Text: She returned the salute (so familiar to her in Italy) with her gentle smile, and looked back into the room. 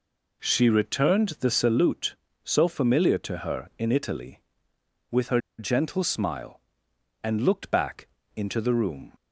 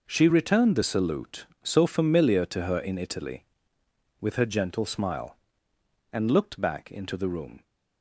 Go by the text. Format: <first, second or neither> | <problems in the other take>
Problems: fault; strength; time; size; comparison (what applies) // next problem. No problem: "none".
second | pauses between "her" and "gentle"; slight; at 5.3 s; 0.19 s long // pauses between "back" and "into"; slight; at 8.0 s; 0.26 s long